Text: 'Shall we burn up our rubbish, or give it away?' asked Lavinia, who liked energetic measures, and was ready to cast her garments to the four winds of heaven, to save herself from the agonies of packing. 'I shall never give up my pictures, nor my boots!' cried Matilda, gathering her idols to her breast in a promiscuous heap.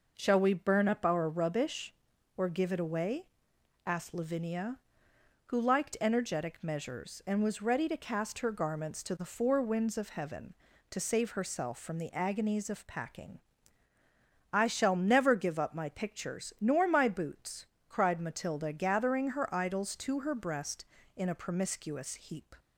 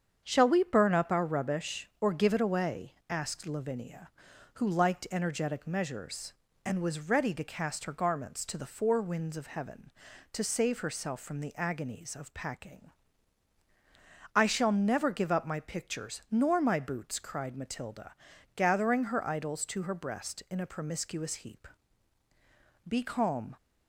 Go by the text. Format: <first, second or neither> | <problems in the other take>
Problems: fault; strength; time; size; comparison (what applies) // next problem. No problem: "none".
first | starts louder than the rest; strong; until 1.2 s; 7.5 dB // goes on to say "Be calm"; noticeable; from 22.8 s on; 0.70 s long